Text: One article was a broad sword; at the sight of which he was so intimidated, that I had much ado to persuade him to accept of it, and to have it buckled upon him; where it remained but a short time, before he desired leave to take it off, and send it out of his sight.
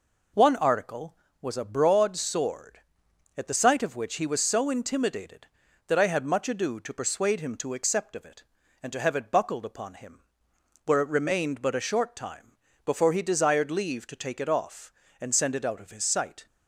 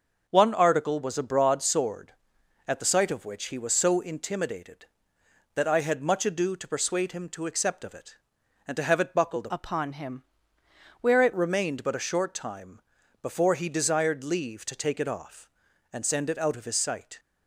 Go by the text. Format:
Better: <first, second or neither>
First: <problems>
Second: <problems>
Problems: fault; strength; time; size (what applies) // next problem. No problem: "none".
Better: first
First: none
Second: starts louder than the rest; until 1.3 s; 6 dB // changes voice from "upon" to "it"; from 9.4 to 11.3 s; 1.9 s long